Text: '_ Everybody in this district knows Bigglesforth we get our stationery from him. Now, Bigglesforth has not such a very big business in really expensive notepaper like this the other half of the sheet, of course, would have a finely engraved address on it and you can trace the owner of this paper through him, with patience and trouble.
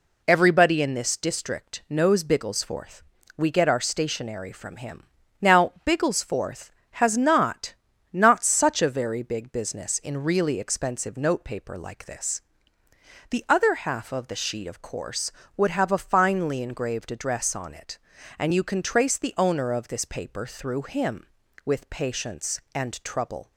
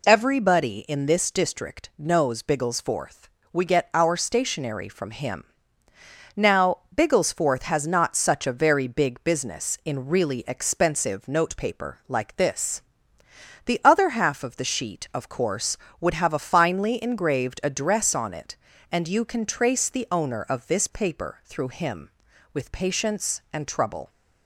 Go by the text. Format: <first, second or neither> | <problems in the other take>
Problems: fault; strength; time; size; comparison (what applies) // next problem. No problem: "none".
second | pauses between "Bigglesforth" and "we"; slight; at 3.0 s; 0.34 s long; slight in the second // says "not" twice; at 8.0 s // pauses between "this" and "the"; noticeable; at 12.3 s; 0.92 s long; noticeable in the second